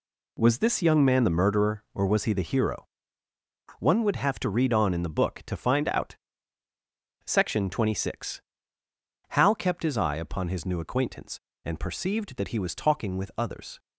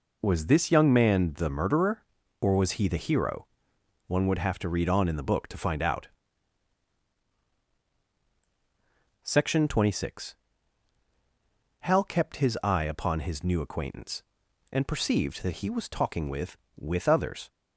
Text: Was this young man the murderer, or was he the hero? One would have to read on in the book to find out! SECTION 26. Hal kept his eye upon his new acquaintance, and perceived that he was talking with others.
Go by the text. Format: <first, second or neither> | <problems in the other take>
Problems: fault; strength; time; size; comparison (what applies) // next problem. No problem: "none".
first | says "with" twice; at 16.7 s